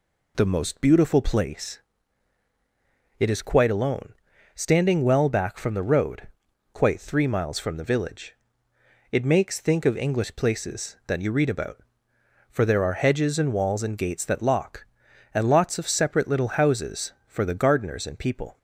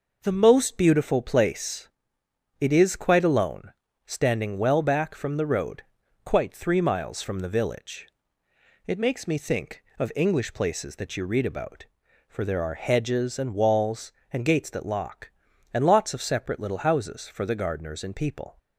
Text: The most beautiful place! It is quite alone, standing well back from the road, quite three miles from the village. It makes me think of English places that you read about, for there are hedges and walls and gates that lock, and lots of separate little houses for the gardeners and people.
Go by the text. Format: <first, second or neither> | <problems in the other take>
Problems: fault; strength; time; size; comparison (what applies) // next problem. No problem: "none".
second | skips "me"; at 9.5 s